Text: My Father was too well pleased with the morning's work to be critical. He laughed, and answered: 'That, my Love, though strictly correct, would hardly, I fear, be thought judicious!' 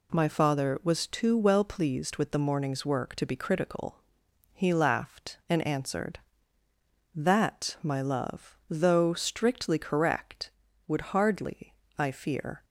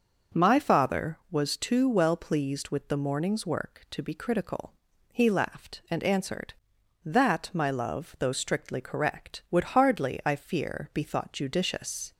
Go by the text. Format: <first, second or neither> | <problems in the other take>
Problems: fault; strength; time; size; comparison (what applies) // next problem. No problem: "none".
second | stops before "be thought judicious"; at 12.6 s